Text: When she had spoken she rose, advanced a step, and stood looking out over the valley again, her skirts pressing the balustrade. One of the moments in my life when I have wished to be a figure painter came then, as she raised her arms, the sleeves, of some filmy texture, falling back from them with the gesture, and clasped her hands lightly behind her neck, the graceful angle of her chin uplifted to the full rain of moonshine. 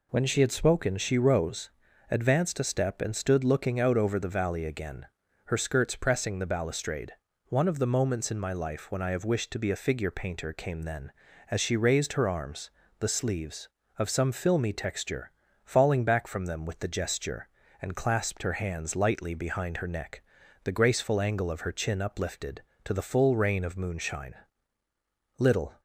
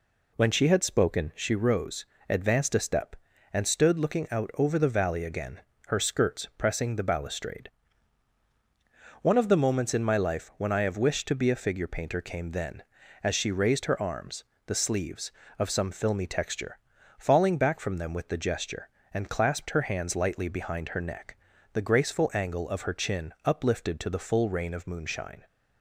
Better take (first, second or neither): second